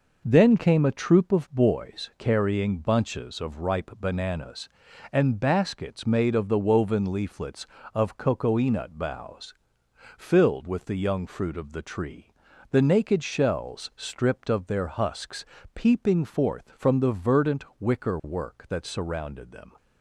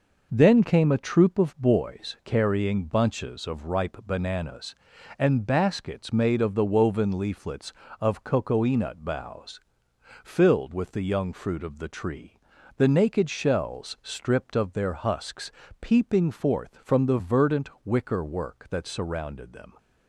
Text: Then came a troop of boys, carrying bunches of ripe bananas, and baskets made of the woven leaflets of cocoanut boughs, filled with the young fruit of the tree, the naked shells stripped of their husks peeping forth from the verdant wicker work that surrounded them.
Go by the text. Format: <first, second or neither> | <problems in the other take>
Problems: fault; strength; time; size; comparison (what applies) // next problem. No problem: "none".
neither | pauses between "husks" and "peeping"; slight; the same in both